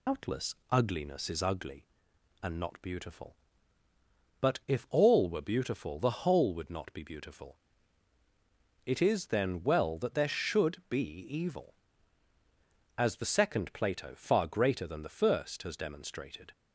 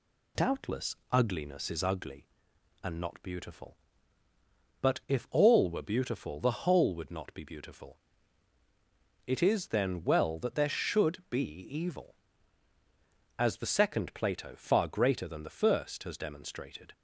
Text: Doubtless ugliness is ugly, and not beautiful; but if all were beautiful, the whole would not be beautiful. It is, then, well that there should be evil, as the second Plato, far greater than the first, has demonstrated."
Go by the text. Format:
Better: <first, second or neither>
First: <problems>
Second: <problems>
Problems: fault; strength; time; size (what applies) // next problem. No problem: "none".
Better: second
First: loses the start of "Doubtless"; at 0.0 s; 125 ms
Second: none